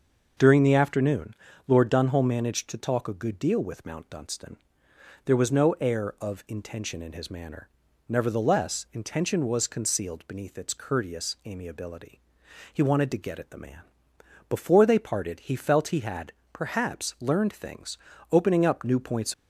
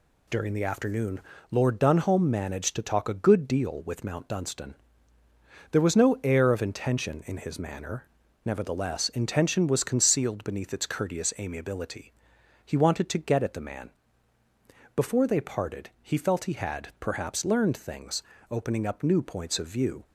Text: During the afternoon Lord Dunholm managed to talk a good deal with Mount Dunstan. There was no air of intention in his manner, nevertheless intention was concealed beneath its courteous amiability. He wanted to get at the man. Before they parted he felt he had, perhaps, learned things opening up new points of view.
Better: second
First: pauses between "afternoon" and "Lord"; slight; at 1.3 s; 0.32 s long // pauses between "things" and "opening"; slight; at 17.9 s; 0.32 s long // stops before "of view"; at 19.3 s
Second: pauses between "afternoon" and "Lord"; slight; at 1.2 s; 0.30 s long // pauses between "things" and "opening"; slight; at 18.2 s; 0.30 s long

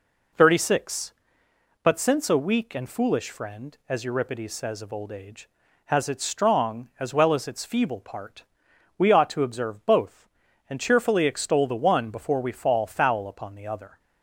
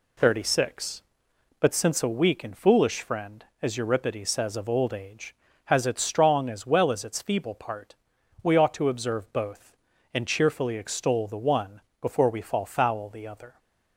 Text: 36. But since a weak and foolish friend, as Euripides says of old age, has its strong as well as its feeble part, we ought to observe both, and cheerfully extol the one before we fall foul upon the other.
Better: first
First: none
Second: pauses between "one" and "before"; slight; at 11.8 s; 0.18 s long // skips "upon"; at 13.0 s

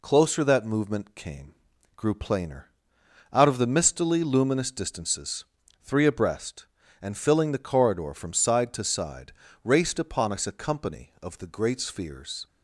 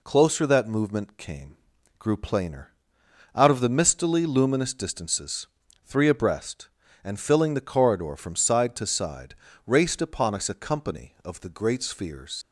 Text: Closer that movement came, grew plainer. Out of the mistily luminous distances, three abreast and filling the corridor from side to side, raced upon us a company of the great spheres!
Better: first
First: none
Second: leaves "spheres" unfinished; at 12.4 s; 70 ms

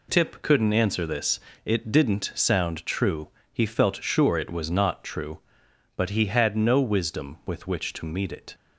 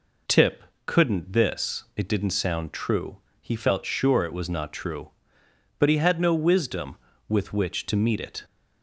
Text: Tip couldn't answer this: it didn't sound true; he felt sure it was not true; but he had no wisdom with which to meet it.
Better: first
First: none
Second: pauses between "Tip" and "couldn't"; slight; at 0.6 s; 0.22 s long // skips "answer"; at 1.3 s

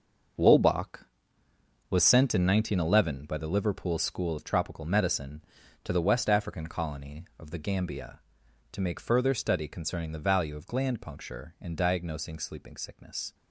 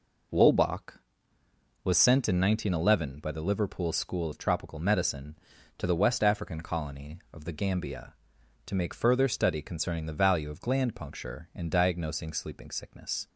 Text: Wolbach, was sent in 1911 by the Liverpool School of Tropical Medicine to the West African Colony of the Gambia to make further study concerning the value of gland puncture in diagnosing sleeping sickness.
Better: second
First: gets quieter; strong; throughout; 10.5 dB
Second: none

